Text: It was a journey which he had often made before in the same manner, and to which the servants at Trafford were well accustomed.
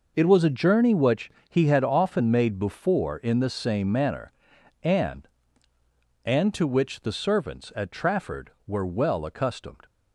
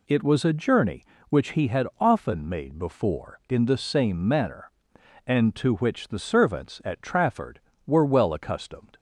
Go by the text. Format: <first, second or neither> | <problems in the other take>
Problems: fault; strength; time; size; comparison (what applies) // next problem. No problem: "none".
second | pauses between "which" and "he"; slight; at 1.2 s; 0.20 s long // says "and" twice; at 6.2 s